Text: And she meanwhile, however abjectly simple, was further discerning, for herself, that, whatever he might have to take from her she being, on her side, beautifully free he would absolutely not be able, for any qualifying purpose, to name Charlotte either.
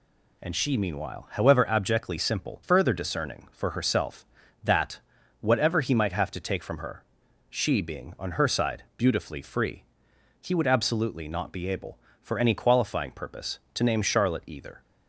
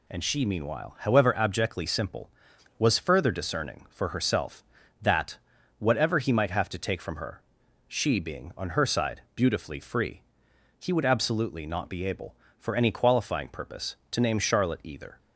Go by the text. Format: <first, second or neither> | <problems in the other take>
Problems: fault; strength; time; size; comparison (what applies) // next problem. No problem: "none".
second | skips "was"; at 2.6 s // pauses between "her" and "she"; noticeable; at 7.0 s; 0.46 s long; noticeable in the second // pauses between "free" and "he"; noticeable; at 9.8 s; 0.58 s long; noticeable in the second